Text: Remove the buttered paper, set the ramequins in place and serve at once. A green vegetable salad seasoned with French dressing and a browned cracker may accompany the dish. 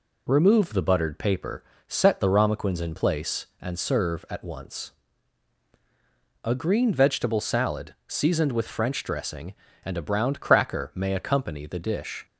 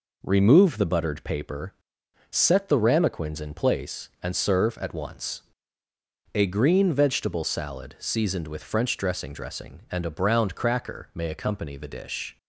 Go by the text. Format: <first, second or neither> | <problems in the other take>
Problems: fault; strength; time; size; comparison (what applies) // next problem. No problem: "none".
first | says "dressing" twice; at 9.3 s